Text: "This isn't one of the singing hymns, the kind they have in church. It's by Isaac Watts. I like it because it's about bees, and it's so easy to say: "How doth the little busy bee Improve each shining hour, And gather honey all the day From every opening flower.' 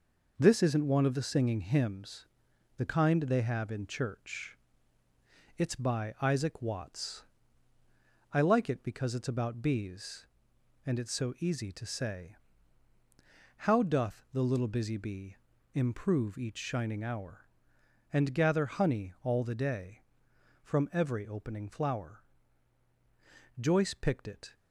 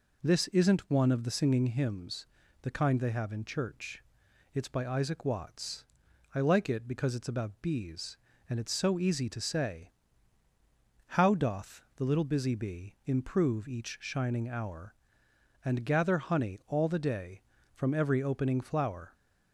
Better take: second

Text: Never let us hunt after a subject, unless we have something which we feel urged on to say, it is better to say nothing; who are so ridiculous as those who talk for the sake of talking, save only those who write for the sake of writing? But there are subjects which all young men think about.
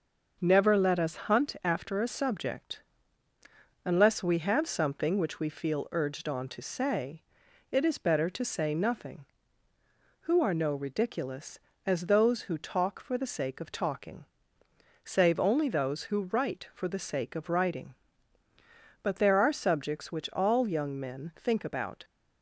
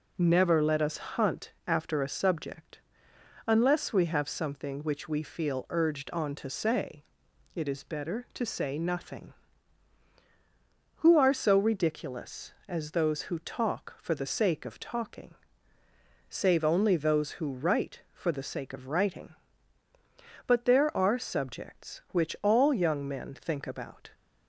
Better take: second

